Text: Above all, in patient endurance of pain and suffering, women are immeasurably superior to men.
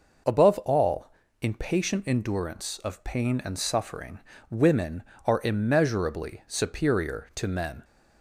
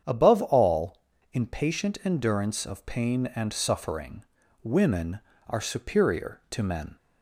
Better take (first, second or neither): first